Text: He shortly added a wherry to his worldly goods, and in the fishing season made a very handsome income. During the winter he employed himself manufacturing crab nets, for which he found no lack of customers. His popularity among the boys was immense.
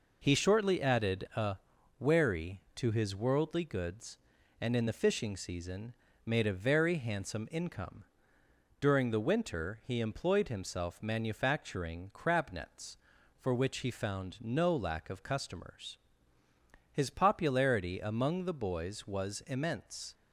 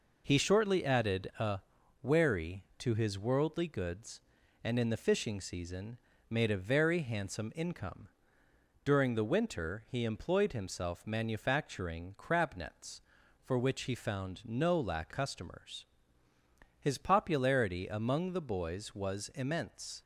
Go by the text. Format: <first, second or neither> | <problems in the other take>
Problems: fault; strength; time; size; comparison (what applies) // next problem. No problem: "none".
first | pauses between "a" and "wherry"; at 1.5 s; 0.42 s long; also in the first // pauses between "season" and "made"; slight; at 5.9 s; 0.34 s long; slight in the first // skips "of"; at 15.1 s